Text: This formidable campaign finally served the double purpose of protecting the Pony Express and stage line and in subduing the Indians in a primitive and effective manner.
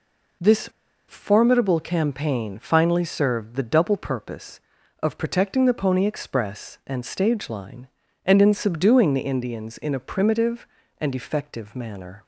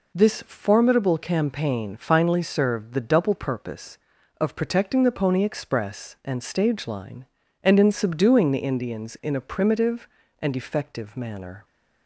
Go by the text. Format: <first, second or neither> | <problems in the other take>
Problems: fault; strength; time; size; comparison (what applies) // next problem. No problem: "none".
second | pauses between "This" and "formidable"; at 0.6 s; 0.42 s long